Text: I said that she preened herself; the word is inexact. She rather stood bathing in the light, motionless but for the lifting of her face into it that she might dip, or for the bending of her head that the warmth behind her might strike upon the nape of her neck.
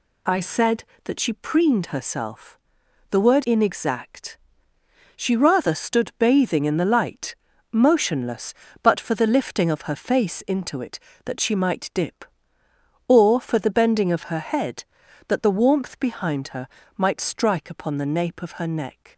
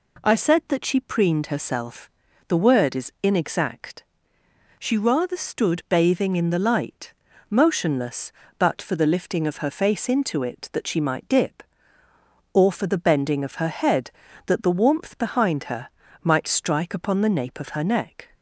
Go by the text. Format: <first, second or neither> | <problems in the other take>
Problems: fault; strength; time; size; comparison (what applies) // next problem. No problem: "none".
second | skips "is"; at 3.4 s // pauses between "her" and "might"; slight; at 16.6 s; 0.32 s long; slight in the second